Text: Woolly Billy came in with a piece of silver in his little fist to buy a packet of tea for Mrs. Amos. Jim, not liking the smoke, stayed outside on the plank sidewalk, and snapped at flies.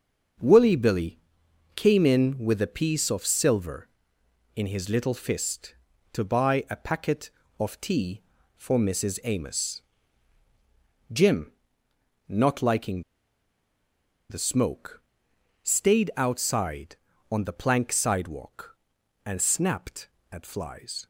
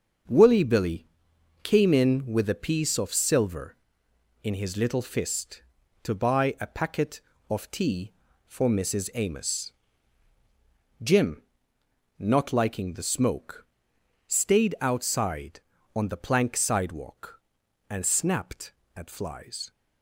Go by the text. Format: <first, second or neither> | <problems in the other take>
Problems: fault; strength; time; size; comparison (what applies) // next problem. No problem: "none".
second | starts louder than the rest; until 1.9 s; 6.5 dB; also in the second // pauses between "Billy" and "came"; noticeable; at 1.1 s; 0.56 s long; noticeable in the second // pauses between "liking" and "the"; strong; at 13.0 s; 1.2 s long